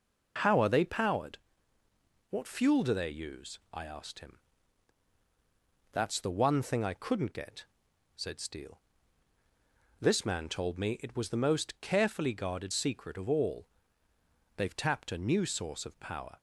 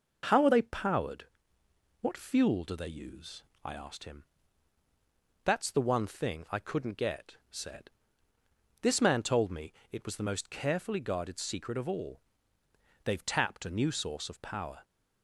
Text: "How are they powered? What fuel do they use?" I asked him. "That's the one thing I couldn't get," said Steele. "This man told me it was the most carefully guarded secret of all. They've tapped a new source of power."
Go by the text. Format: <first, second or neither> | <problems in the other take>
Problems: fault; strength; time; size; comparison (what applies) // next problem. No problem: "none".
first | skips "Steele"; at 8.3 s // pauses between "me" and "it"; slight; at 9.7 s; 0.18 s long